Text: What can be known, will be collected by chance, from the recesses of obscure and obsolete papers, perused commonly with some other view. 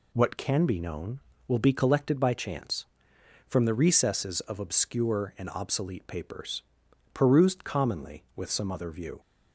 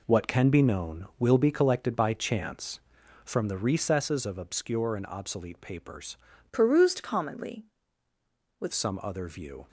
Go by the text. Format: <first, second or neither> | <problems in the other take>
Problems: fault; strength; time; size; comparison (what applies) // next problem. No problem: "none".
first | changes voice from "perused" to "with"; from 6.5 to 8.7 s; 2.2 s long